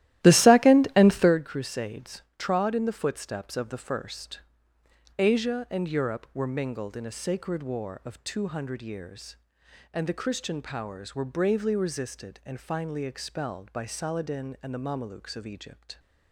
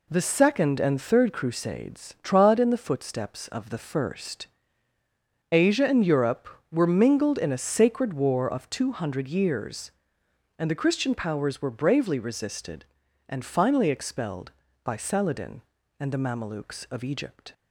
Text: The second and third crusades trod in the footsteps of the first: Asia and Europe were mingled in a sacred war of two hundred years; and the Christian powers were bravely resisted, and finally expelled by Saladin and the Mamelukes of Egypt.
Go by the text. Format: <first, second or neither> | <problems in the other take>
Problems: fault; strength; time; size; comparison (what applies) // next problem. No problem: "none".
second | starts louder than the rest; strong; until 1.4 s; 14.5 dB